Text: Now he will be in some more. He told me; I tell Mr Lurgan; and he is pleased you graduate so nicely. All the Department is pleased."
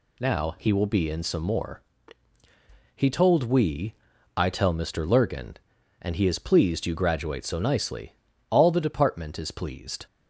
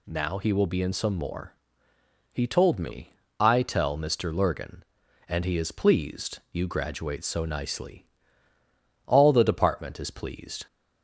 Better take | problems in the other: second | says "we" for "me"; at 3.4 s

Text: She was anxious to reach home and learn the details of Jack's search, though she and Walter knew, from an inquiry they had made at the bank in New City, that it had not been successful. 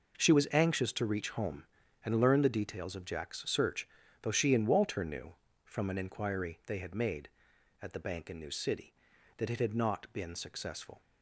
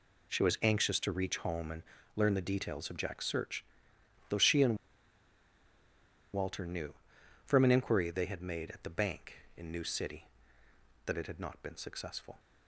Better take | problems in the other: first | pauses between "and" and "learn"; slight; at 1.8 s; 0.32 s long // pauses between "and" and "Walter"; strong; at 4.7 s; 1.5 s long

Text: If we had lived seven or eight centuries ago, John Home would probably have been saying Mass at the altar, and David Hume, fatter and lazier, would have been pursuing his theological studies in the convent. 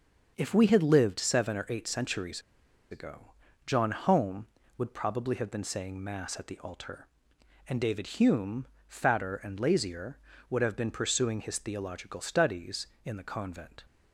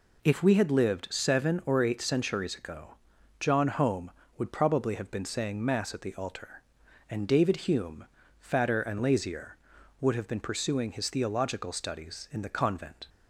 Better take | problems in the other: second | starts louder than the rest; until 1.3 s; 6.5 dB // pauses between "centuries" and "ago"; noticeable; at 2.4 s; 0.50 s long

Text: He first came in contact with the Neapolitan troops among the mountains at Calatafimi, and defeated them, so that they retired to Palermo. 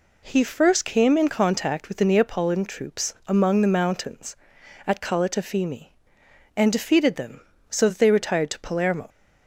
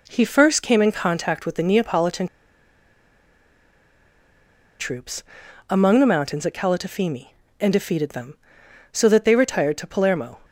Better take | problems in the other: first | pauses between "Neapolitan" and "troops"; strong; at 2.2 s; 2.5 s long // pauses between "troops" and "among"; noticeable; at 5.2 s; 0.48 s long

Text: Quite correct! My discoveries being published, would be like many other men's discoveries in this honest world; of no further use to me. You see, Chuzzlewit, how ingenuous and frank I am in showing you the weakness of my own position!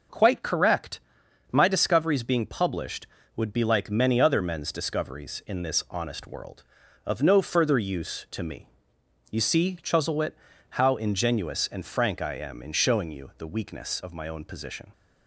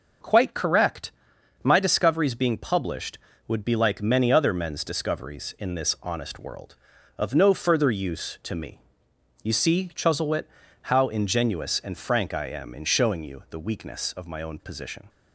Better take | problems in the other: neither | none

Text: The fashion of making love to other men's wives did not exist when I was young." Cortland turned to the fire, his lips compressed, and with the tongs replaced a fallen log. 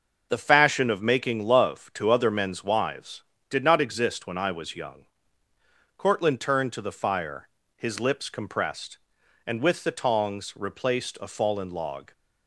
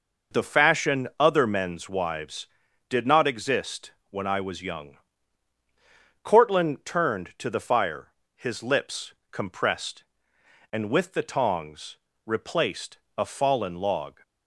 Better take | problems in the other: first | skips "of making love to"; at 1.1 s // pauses between "exist" and "when"; slight; at 3.9 s; 0.16 s long // pauses between "lips" and "compressed"; slight; at 9.1 s; 0.18 s long // pauses between "tongs" and "replaced"; slight; at 11.9 s; 0.26 s long // pauses between "replaced" and "a"; slight; at 12.9 s; 0.22 s long

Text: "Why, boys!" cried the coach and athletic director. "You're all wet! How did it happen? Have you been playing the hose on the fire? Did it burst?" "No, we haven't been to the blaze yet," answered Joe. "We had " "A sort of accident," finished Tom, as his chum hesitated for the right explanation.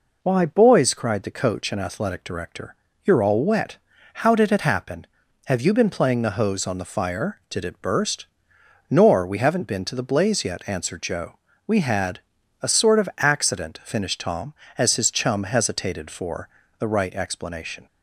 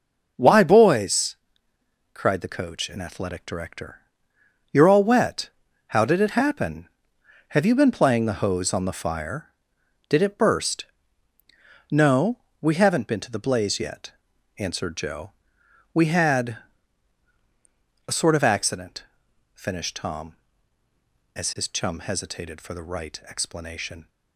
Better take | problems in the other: second | says "Nor" for "No"; at 8.8 s // pauses between "for" and "the"; slight; at 16.4 s; 0.32 s long

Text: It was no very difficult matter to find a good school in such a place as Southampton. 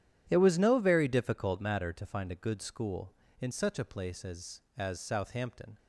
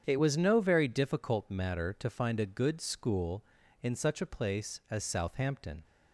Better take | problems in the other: second | starts louder than the rest; strong; until 1.3 s; 10.5 dB; strong in the second // says "as" twice; at 4.7 s

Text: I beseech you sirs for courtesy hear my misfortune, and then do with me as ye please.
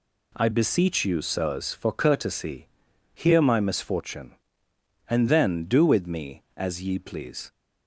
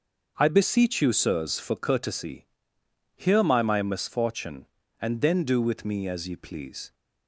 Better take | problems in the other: first | starts louder than the rest; until 1.3 s; 6.5 dB // pauses between "courtesy" and "hear"; noticeable; at 2.4 s; 0.68 s long; noticeable in the first // says "my" twice; at 3.6 s

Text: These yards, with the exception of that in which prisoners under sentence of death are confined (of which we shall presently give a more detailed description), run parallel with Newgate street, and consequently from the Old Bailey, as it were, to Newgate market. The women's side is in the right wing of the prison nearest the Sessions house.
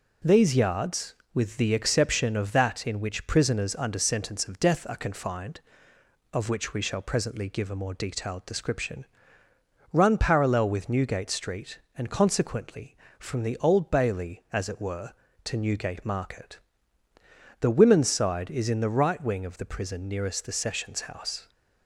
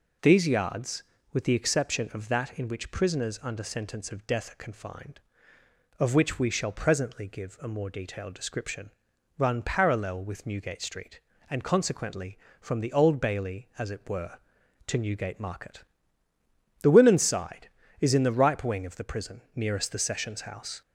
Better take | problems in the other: first | says "ripe" for "right"; at 18.3 s // pauses between "prison" and "nearest"; slight; at 19.3 s; 0.16 s long

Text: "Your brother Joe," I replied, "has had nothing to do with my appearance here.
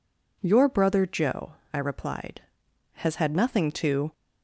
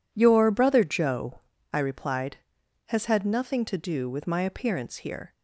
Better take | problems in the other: second | stops before "do with my appearance here"; at 4.1 s

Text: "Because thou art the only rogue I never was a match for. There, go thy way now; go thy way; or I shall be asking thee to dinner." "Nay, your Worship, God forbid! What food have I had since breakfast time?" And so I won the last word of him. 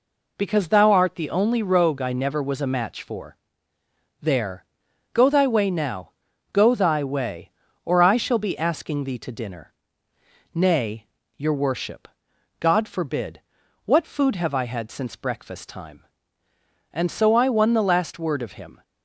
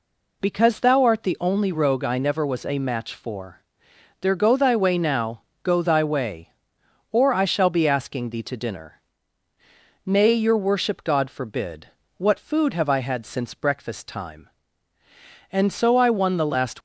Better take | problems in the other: first | stops before "word of him"; at 16.7 s

